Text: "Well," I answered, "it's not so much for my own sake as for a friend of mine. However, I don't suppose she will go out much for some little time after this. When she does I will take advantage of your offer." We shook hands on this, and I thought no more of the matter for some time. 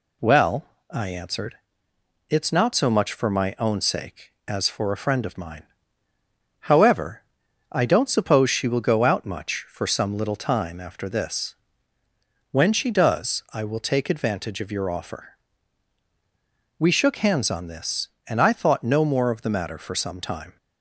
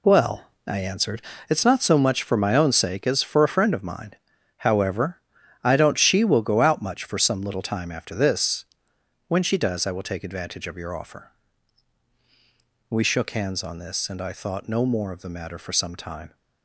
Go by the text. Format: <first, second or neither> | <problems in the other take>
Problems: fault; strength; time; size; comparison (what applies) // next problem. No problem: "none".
first | skips "suppose"; at 5.9 s